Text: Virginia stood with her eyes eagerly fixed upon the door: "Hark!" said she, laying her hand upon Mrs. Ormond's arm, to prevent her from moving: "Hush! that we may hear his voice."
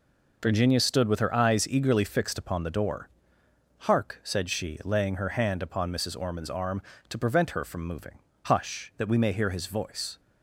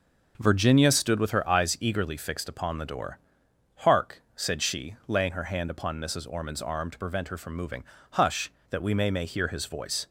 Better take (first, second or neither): first